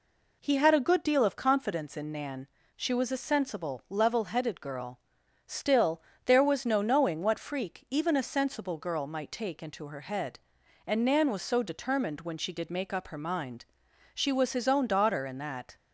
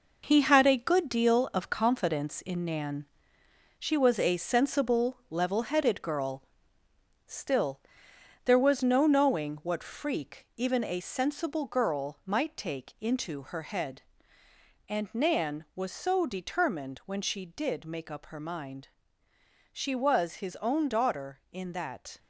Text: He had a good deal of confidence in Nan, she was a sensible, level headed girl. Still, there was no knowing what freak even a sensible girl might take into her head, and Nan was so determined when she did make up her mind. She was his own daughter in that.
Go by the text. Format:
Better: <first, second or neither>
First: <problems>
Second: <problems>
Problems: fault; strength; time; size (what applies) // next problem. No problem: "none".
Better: first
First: none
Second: gets quieter; strong; throughout; 7 dB